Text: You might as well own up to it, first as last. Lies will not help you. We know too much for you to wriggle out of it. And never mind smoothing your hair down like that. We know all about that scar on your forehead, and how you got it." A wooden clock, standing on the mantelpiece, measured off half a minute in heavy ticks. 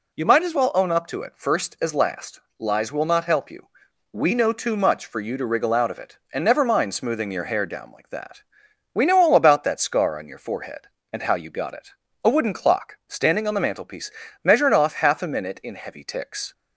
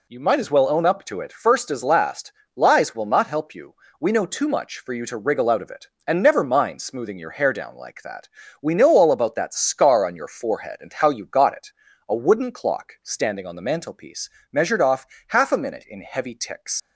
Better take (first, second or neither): first